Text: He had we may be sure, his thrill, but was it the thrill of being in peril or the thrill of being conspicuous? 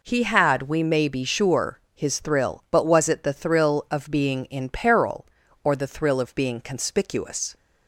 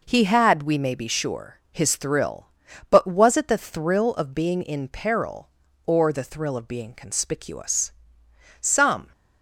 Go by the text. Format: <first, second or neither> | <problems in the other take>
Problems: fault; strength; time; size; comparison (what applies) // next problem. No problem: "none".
first | goes on to say "Some"; from 8.5 s on; 0.52 s long